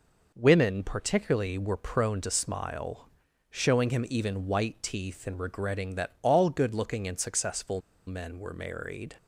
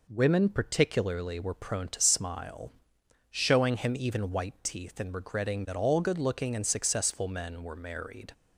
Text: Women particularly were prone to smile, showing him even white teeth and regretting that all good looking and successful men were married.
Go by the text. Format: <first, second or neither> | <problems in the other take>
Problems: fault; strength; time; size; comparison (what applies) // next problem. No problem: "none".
second | pauses between "successful" and "men"; slight; at 7.8 s; 0.26 s long